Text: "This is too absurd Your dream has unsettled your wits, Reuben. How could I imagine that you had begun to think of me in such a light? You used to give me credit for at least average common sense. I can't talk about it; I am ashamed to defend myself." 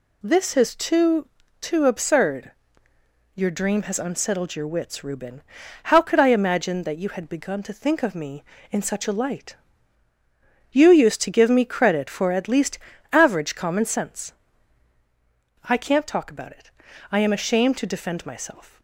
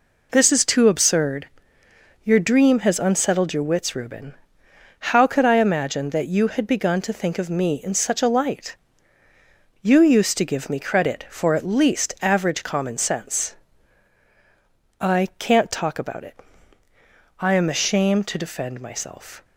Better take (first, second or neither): second